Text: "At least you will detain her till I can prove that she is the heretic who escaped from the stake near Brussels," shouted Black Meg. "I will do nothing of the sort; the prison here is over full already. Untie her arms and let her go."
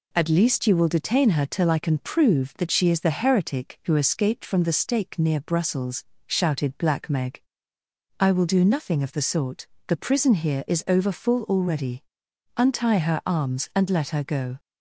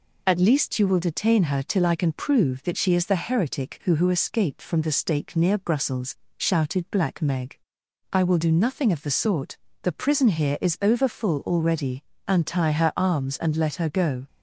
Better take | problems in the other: first | says "who" twice; at 3.9 s

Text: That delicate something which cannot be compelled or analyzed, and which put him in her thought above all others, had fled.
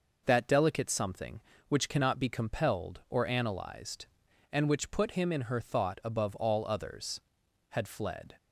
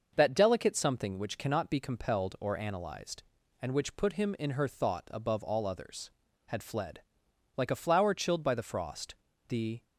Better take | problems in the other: first | starts louder than the rest; until 1.1 s; 6 dB // goes on to say "Like a flower chilled by the frost the"; strong; from 7.5 s on; 2.2 s long

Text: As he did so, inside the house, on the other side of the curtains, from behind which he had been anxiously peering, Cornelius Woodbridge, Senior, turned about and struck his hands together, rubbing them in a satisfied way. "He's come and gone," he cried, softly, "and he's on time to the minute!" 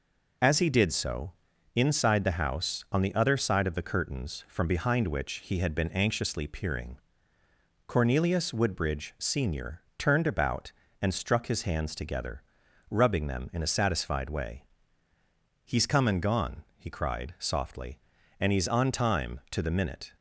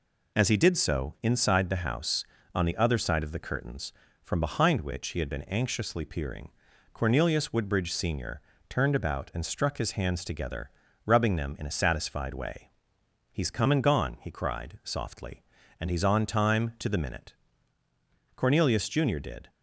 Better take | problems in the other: first | goes on to say "Cornelius Junior did"; noticeable; from 18.3 s on; 1.1 s long

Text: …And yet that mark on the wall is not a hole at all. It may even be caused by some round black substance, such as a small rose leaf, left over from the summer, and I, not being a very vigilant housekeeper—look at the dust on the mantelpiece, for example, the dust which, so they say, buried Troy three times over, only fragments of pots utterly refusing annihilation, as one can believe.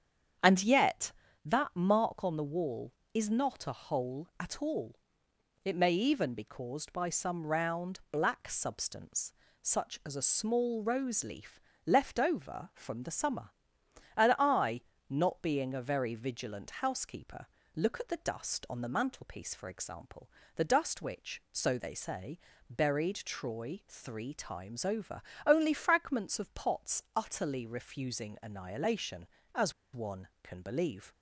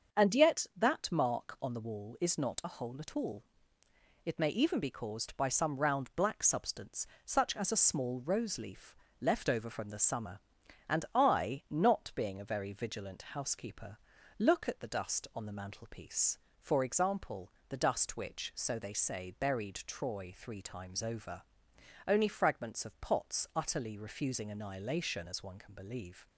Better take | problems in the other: second | starts louder than the rest; strong; until 1.7 s; 8.5 dB; also in the second // pauses between "as" and "one"; slight; at 29.7 s; 0.20 s long

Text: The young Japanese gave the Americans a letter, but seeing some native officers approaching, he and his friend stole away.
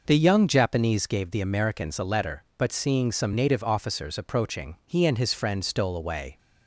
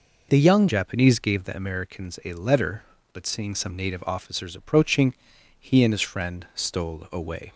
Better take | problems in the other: first | changes voice at "Japanese"; from 0.6 s on; 6.9 s long

